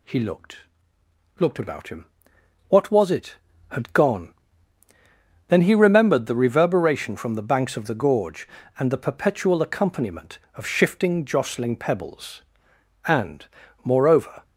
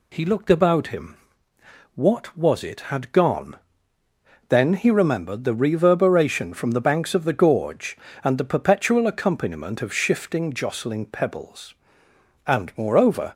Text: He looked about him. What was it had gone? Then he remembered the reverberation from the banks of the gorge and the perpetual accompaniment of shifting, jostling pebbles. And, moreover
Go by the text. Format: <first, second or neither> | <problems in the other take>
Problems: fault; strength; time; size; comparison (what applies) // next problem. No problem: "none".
second | says "looked" twice; at 1.4 s